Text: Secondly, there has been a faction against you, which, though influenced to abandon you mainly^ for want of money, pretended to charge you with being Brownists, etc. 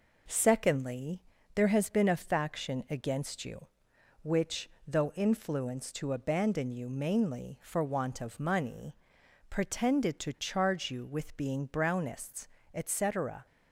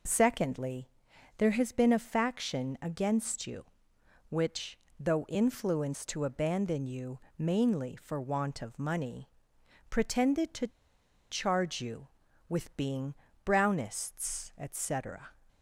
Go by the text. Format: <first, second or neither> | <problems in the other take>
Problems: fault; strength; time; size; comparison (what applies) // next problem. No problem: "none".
first | pauses between "you" and "mainly"; slight; at 7.1 s; 0.18 s long // pauses between "to" and "charge"; noticeable; at 10.6 s; 0.62 s long // pauses between "being" and "Brownists"; slight; at 13.1 s; 0.30 s long